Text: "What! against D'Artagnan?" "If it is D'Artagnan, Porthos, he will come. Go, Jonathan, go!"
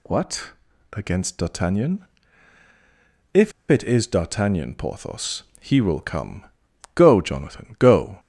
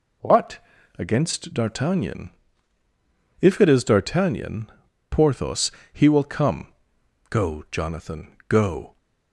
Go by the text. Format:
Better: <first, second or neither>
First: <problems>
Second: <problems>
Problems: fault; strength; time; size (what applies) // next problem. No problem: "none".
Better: second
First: pauses between "If" and "it"; slight; at 3.5 s; 0.17 s long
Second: none